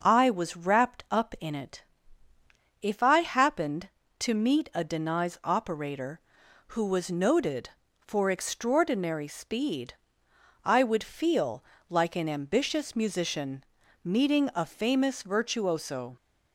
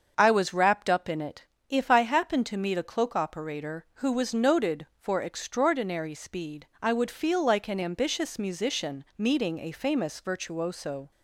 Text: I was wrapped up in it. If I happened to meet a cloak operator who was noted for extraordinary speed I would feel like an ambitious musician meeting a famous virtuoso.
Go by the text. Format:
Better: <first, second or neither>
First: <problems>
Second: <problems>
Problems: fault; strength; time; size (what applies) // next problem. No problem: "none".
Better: second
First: starts louder than the rest; noticeable; until 1.0 s; 6 dB // says "denies" for "cloak"; at 4.8 s // pauses between "speed" and "I"; noticeable; at 9.9 s; 0.70 s long // pauses between "feel" and "like"; slight; at 11.6 s; 0.28 s long // pauses between "musician" and "meeting"; at 13.6 s; 0.40 s long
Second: starts louder than the rest; until 1.2 s; 6.5 dB // pauses between "speed" and "I"; slight; at 6.6 s; 0.16 s long